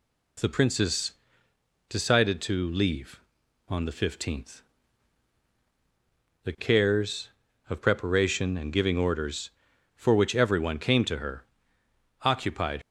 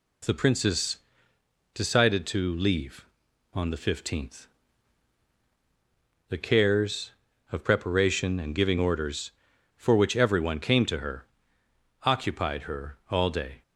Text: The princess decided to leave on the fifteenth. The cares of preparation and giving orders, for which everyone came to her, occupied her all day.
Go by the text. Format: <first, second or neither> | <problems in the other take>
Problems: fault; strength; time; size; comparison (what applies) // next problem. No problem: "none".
second | pauses between "princess" and "decided"; noticeable; at 1.1 s; 0.74 s long; noticeable in the second // stops before "her all day"; at 12.8 s